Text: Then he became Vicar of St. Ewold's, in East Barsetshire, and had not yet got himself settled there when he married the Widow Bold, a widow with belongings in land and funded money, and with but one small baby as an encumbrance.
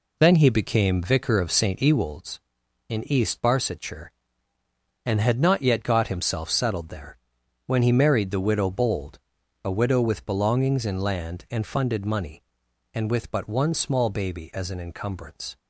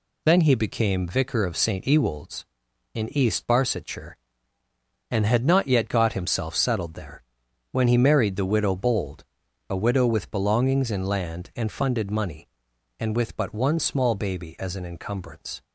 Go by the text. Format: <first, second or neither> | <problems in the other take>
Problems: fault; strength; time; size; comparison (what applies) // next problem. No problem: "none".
second | starts louder than the rest; slight; until 2.0 s; 3 dB // pauses between "there" and "when"; noticeable; at 7.1 s; 0.48 s long; noticeable in the second